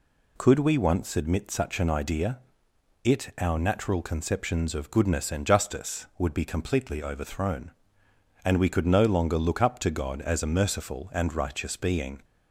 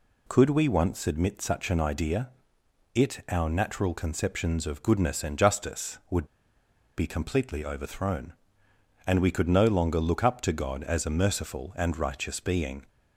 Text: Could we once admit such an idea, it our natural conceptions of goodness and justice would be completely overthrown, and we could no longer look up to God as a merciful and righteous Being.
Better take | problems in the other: first | pauses between "would" and "be"; noticeable; at 6.2 s; 0.71 s long

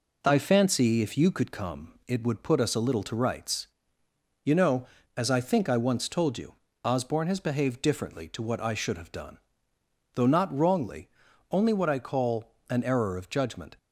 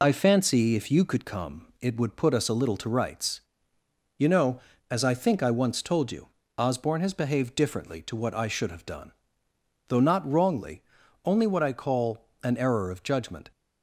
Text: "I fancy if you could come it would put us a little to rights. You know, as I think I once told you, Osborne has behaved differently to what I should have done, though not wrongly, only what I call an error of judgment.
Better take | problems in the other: first | loses the start of "I"; at 0.0 s; 45 ms // pauses between "call" and "an"; slight; at 12.2 s; 0.16 s long; slight in the first

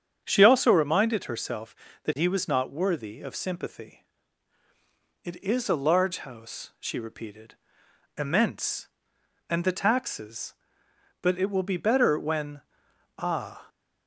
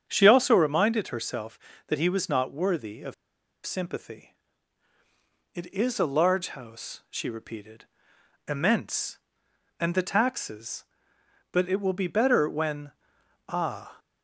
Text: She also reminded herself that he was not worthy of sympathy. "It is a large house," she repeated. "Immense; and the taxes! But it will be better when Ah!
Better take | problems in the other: first | starts louder than the rest; strong; until 1.0 s; 8 dB; strong in the first // pauses between "of" and "sympathy"; noticeable; at 3.1 s; 0.52 s long // pauses between "when" and "Ah"; noticeable; at 12.9 s; 0.58 s long; noticeable in the first

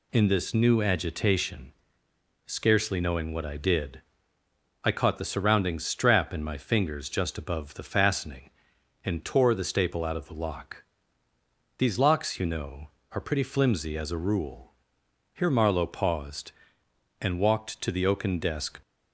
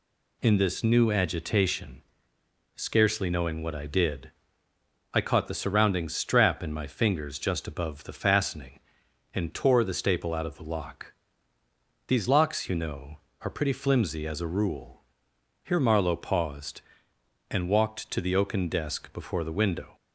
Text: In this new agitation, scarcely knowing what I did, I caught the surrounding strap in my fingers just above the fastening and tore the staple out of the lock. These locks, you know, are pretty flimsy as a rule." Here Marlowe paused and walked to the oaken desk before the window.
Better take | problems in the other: second | stops before "before the window"; at 18.8 s

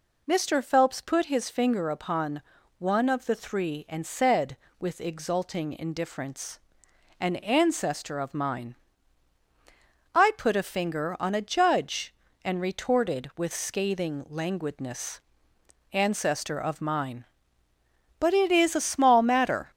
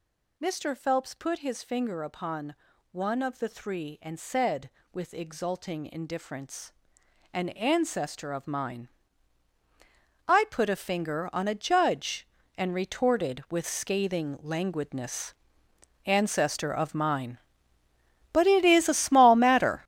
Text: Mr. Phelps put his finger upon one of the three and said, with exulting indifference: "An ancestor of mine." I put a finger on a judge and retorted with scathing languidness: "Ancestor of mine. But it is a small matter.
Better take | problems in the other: first | gets louder; strong; throughout; 11.5 dB // pauses between "upon" and "one"; slight; at 2.5 s; 0.36 s long; slight in the first

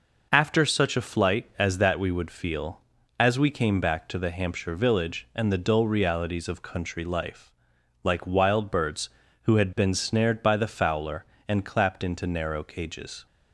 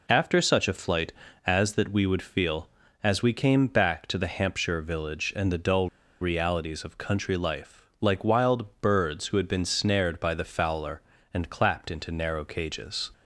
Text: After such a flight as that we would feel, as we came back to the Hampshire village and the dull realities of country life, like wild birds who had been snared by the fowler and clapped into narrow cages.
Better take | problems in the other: first | pauses between "dull" and "realities"; slight; at 5.8 s; 0.32 s long

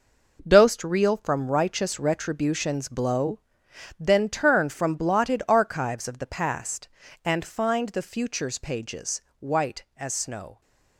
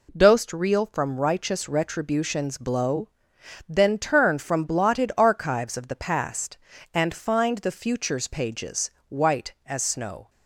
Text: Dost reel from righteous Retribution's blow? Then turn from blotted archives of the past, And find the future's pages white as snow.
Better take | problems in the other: second | gets quieter; strong; throughout; 9.5 dB // pauses between "pages" and "white"; slight; at 9.2 s; 0.18 s long; slight in the second

